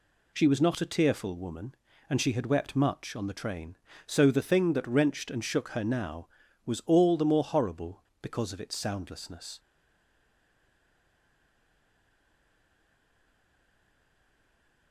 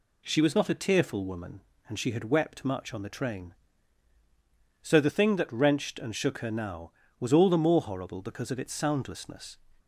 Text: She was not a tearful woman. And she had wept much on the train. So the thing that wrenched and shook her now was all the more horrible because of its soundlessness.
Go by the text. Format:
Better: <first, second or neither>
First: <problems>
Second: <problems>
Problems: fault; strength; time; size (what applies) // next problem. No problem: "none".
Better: second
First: stays silent after the last word; strong; from 9.5 s on; 5.4 s long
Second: none